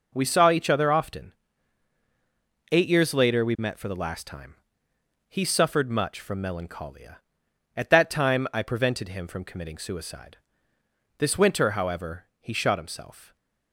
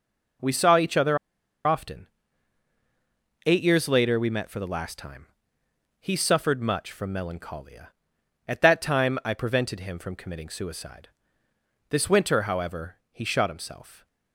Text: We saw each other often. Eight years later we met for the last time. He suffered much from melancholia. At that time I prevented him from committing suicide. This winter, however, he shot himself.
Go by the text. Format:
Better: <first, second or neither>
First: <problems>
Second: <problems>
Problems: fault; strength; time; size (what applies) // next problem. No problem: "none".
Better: first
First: none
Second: pauses between "other" and "often"; noticeable; at 1.1 s; 0.49 s long